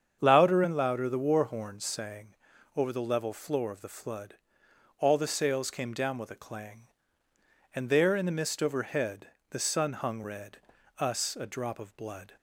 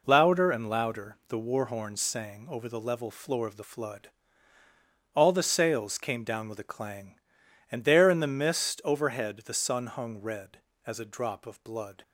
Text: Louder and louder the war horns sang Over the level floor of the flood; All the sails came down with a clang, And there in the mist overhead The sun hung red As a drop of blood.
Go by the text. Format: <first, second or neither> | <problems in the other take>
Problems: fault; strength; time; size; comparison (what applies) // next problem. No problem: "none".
second | starts louder than the rest; strong; until 1.2 s; 7.5 dB // pauses between "sang" and "Over"; noticeable; at 2.2 s; 0.46 s long // pauses between "overhead" and "The"; slight; at 9.2 s; 0.24 s long // says "Us" for "As"; at 10.9 s